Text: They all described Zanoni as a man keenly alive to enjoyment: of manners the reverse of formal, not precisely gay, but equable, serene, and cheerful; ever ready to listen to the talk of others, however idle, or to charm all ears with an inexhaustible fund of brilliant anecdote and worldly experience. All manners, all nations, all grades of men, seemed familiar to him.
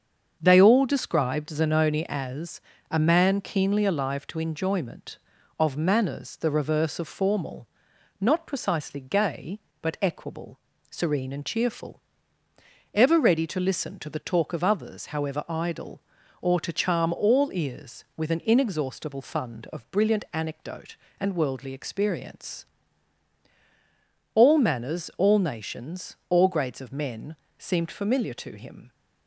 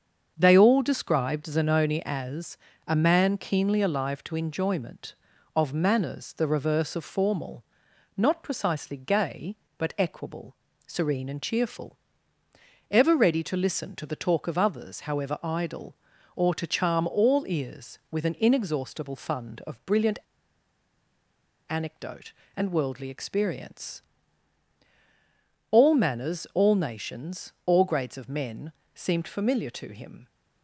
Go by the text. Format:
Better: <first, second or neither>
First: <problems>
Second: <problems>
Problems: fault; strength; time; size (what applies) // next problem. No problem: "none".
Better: first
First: starts louder than the rest; until 1.4 s; 7 dB // pauses between "as" and "a"; slight; at 2.6 s; 0.30 s long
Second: starts louder than the rest; until 1.3 s; 7 dB // pauses between "as" and "a"; slight; at 2.5 s; 0.30 s long // pauses between "brilliant" and "anecdote"; strong; at 20.1 s; 1.5 s long